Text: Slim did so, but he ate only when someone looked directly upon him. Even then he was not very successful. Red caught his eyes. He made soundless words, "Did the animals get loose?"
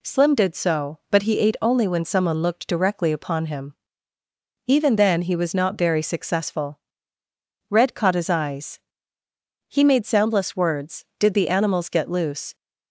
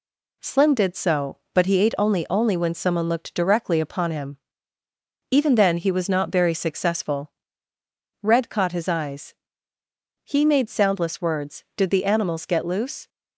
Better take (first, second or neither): first